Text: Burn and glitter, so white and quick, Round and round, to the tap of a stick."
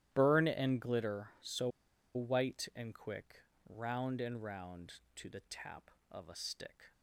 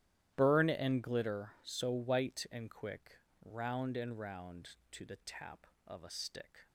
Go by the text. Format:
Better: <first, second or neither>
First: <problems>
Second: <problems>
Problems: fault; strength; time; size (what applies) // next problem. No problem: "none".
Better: second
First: starts louder than the rest; strong; until 1.1 s; 12.5 dB // pauses between "so" and "white"; at 1.6 s; 0.45 s long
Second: starts louder than the rest; strong; until 1.3 s; 12.5 dB